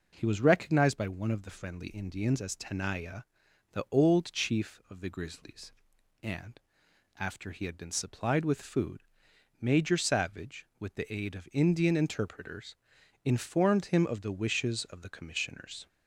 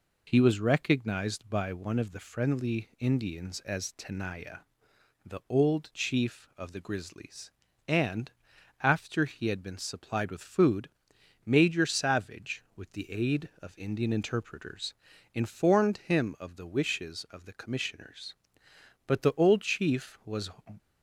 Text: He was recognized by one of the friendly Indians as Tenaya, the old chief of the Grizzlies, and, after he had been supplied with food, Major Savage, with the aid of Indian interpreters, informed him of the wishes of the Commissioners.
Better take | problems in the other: first | goes on to say "But the old chief was"; from 19.0 s on; 1.4 s long

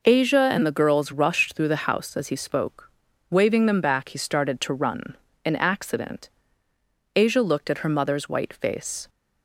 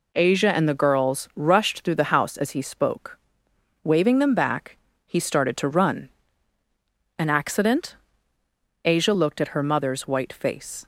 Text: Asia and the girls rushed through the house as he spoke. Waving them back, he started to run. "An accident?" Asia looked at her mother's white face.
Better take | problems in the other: neither | none

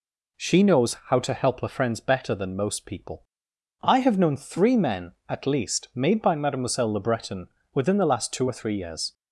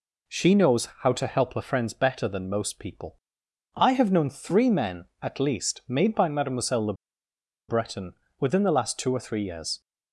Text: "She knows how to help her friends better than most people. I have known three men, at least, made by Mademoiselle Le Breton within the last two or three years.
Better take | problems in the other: first | pauses between "Le" and "Breton"; noticeable; at 6.9 s; 0.74 s long // pauses between "Breton" and "within"; slight; at 8.1 s; 0.26 s long; slight in the first

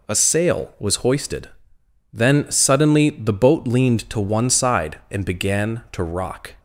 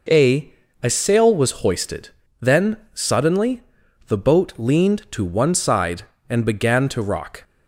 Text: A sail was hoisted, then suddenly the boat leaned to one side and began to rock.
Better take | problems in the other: first | says "A" twice; at 0.8 s // pauses between "then" and "suddenly"; slight; at 2.7 s; 0.16 s long // pauses between "suddenly" and "the"; noticeable; at 3.6 s; 0.46 s long

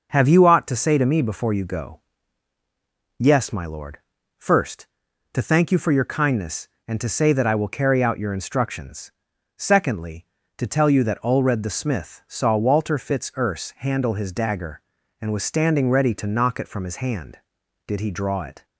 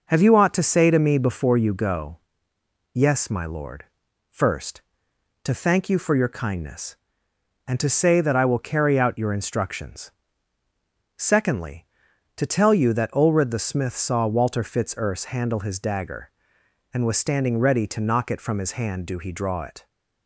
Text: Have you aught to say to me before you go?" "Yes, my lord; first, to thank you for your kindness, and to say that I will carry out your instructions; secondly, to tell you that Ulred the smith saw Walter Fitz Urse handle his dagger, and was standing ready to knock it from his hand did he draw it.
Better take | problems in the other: first | says "do" for "did"; at 19.0 s

